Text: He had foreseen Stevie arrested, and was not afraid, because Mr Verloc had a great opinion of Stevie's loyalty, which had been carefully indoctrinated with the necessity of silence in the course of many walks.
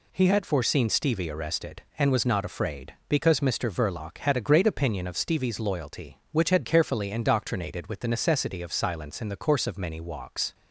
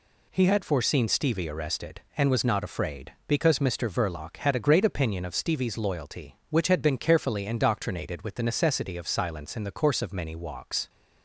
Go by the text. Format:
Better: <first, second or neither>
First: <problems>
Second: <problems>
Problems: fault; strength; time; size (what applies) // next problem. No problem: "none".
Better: second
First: skips "been"; at 6.6 s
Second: none